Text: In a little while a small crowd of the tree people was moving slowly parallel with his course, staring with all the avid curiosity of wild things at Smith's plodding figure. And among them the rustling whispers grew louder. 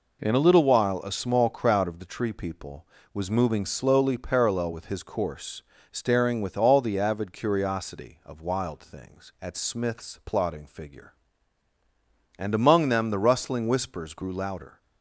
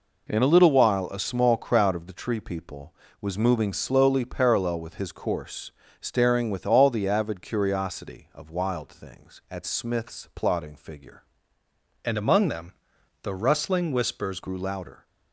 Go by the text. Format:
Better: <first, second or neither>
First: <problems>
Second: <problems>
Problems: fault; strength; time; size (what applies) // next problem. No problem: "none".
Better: first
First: none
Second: changes voice from "And" to "whispers"; from 12.0 to 14.3 s; 2.3 s long // pauses between "them" and "the"; noticeable; at 12.7 s; 0.50 s long